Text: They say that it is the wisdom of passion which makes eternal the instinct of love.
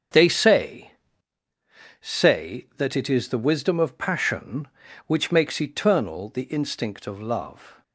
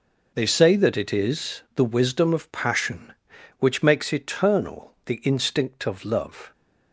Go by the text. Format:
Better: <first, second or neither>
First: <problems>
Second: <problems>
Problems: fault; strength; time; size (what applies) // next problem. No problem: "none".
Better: second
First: starts louder than the rest; strong; until 2.2 s; 7.5 dB // says "say" twice; at 2.0 s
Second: none